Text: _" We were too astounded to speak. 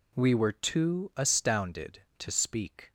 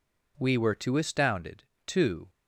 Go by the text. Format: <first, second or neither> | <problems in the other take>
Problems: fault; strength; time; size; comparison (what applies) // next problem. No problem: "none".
first | stops before "speak"; at 2.2 s